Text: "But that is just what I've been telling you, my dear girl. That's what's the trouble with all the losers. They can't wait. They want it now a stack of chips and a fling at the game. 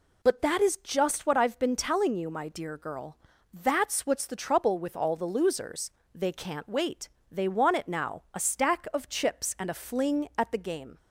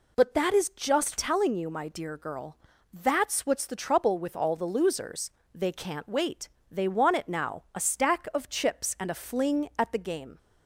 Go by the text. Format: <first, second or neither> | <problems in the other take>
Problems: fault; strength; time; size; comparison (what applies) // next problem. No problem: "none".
first | skips "what I've been"; at 1.1 s